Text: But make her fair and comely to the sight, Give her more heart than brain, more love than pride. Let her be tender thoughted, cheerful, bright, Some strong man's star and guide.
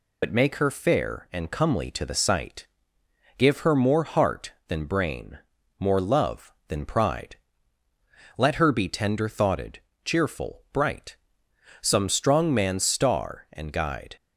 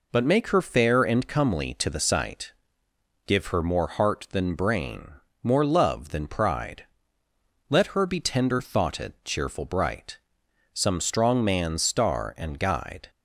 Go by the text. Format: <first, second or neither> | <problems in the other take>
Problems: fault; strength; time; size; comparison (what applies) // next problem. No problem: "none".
second | loses the start of "But"; at 0.2 s; 50 ms